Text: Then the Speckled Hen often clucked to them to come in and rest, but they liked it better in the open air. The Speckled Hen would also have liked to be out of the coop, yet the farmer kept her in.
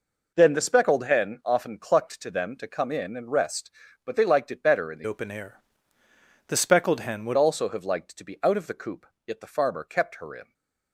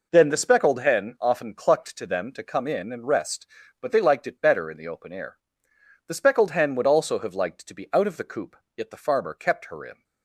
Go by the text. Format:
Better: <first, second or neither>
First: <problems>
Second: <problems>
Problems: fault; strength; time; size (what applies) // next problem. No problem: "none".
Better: second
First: changes voice from "open" to "would"; from 5.0 to 7.3 s; 2.3 s long // stays silent after the last word; slight; from 10.4 s on; 0.5 s long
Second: none